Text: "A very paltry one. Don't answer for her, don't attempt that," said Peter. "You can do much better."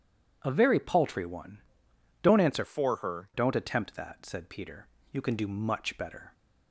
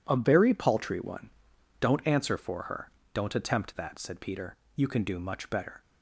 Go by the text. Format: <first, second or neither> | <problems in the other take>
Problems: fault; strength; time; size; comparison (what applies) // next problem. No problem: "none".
second | starts louder than the rest; strong; until 1.4 s; 9 dB // changes voice from "for" to "her"; from 2.6 to 3.2 s; 0.6 s long